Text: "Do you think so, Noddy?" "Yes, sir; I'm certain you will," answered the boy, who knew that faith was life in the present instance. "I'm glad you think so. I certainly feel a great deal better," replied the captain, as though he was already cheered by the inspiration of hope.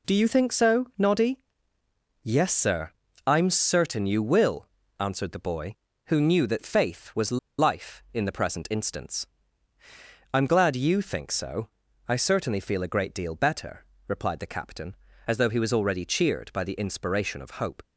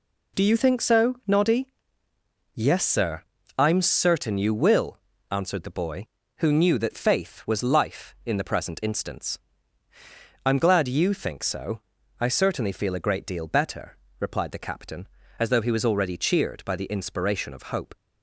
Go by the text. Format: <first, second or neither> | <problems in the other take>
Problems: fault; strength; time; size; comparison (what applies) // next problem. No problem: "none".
second | pauses between "was" and "life"; slight; at 7.3 s; 0.21 s long